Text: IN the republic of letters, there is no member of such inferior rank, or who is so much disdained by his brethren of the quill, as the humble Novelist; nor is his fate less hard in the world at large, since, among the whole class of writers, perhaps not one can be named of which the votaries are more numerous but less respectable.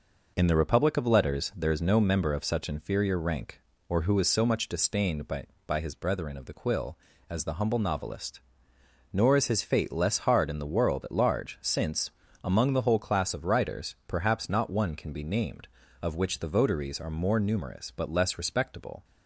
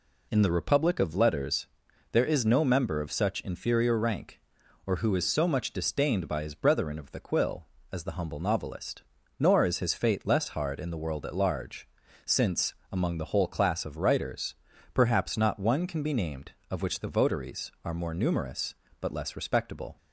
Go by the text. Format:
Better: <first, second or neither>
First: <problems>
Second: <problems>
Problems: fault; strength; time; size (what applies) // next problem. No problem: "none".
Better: second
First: says "by" twice; at 5.6 s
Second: none